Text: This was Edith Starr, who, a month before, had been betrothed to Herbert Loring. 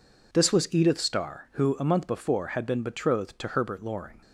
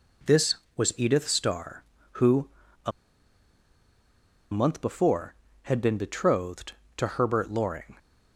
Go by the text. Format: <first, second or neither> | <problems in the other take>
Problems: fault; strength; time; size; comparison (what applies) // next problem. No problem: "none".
first | pauses between "a" and "month"; strong; at 2.9 s; 1.6 s long